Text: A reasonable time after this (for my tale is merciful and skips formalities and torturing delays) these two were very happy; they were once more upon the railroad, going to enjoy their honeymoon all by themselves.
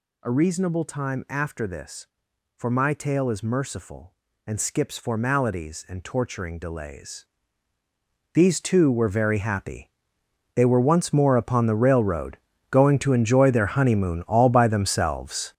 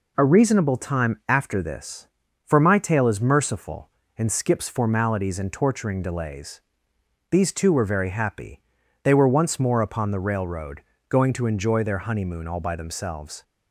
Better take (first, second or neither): second